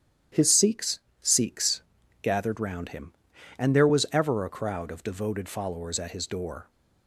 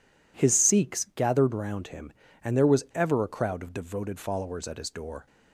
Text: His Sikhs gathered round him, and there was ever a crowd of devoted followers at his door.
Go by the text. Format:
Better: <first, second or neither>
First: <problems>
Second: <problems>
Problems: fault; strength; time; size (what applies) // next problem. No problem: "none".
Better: second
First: starts louder than the rest; strong; until 1.5 s; 10.5 dB // says "Sikhs" twice; at 1.2 s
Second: none